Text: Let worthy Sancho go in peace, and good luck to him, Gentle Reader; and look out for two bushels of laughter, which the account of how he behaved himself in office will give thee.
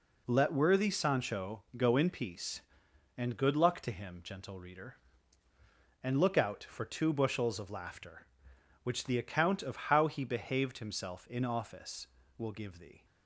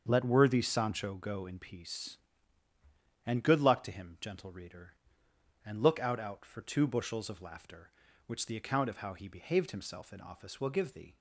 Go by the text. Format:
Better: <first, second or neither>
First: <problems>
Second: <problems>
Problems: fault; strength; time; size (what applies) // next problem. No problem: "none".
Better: first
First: none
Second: starts louder than the rest; until 1.0 s; 7 dB // says "out" twice; at 6.2 s